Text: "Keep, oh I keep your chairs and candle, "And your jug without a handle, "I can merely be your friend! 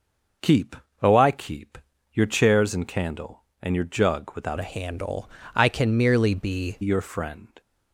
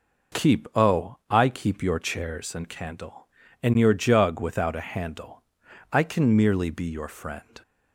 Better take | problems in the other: second | pauses between "keep" and "your"; slight; at 1.7 s; 0.34 s long // changes voice from "a" to "be"; from 4.5 to 6.7 s; 2.2 s long

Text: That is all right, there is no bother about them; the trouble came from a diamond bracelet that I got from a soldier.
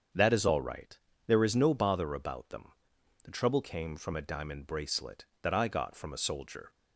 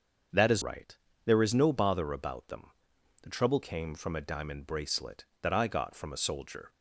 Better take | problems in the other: first | starts louder than the rest; until 1.6 s; 6.5 dB; strong in the first // skips "all"; at 0.6 s

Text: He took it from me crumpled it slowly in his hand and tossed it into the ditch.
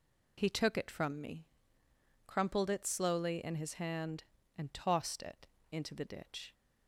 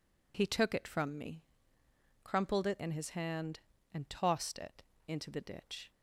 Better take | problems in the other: first | pauses between "me" and "crumpled"; noticeable; at 1.4 s; 0.80 s long; noticeable in the first // skips "slowly"; at 2.7 s // pauses between "it" and "into"; slight; at 4.8 s; 0.26 s long; slight in the first

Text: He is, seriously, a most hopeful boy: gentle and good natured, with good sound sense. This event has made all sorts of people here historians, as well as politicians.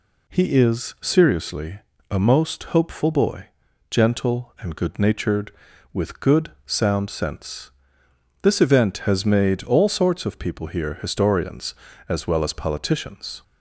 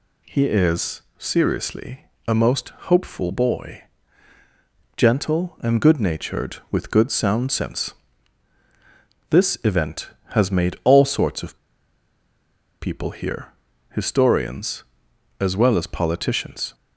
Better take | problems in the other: first | pauses between "most" and "hopeful"; slight; at 2.7 s; 0.18 s long // pauses between "of" and "people"; at 11.5 s; 1.2 s long // pauses between "here" and "historians"; at 13.5 s; 0.40 s long

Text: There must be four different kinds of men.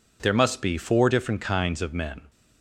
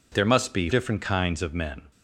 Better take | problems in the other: first | skips "four"; at 0.6 s

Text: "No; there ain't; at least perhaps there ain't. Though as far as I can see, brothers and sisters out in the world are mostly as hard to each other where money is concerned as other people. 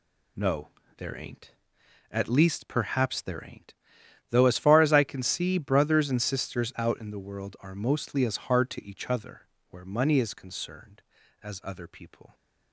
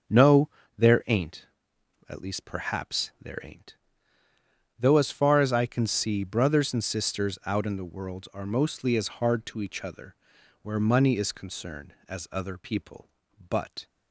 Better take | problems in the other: first | starts louder than the rest; until 1.4 s; 6.5 dB // pauses between "other" and "where"; noticeable; at 10.1 s; 0.48 s long; slight in the first // goes on to say "But"; slight; from 13.4 s on; 0.36 s long

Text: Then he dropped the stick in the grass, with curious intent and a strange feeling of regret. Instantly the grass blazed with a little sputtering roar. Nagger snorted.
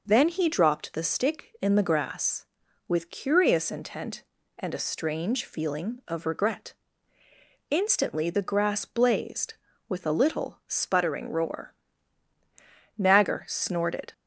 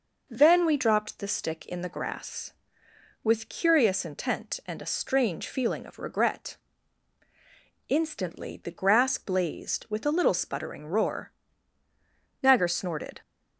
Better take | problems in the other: first | says "we" for "he"; at 0.6 s

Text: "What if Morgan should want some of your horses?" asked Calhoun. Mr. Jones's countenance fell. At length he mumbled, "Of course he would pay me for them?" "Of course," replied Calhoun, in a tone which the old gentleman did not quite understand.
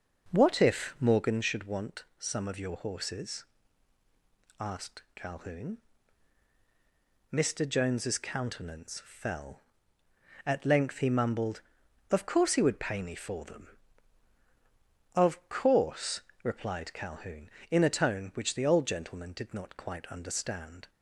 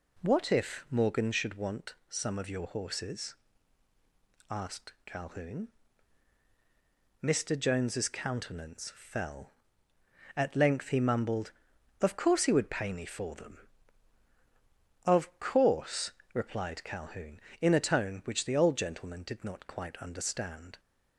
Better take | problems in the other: second | starts louder than the rest; noticeable; until 1.4 s; 5.5 dB // pauses between "want" and "some"; slight; at 2.0 s; 0.16 s long; slight in the second

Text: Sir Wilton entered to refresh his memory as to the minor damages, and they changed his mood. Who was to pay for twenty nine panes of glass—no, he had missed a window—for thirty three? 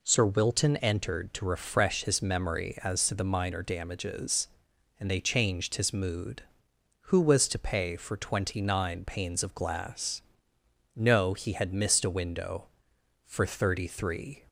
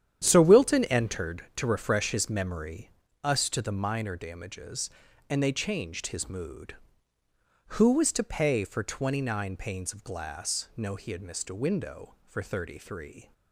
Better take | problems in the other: first | starts louder than the rest; strong; until 1.2 s; 9.5 dB // says "us" for "as"; at 3.2 s

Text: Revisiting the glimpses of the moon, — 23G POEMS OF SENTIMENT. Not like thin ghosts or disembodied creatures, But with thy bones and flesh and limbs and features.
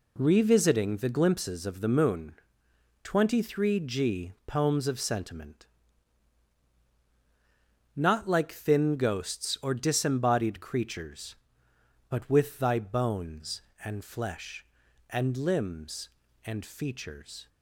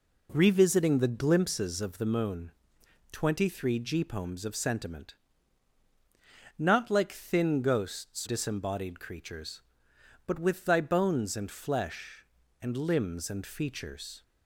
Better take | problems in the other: first | skips "or"; at 8.2 s

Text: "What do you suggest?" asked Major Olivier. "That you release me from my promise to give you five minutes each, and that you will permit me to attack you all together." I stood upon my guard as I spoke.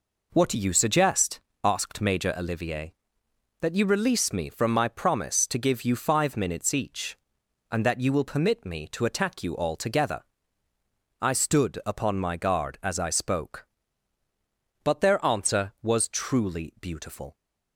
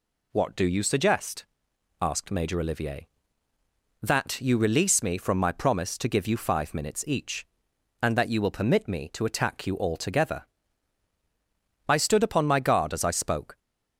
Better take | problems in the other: second | goes on to say "But their answer was truly beautiful"; strong; from 14.8 s on; 2.5 s long

